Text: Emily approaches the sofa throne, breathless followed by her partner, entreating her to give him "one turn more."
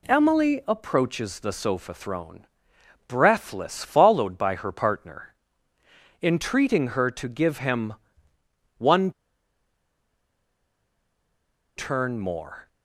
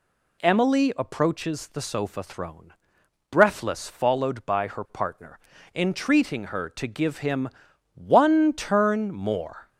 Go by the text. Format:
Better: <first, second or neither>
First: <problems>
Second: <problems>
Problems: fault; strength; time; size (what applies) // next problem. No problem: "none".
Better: second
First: pauses between "him" and "one"; noticeable; at 7.9 s; 0.82 s long // pauses between "one" and "turn"; strong; at 9.1 s; 2.6 s long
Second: pauses between "him" and "one"; noticeable; at 7.4 s; 0.46 s long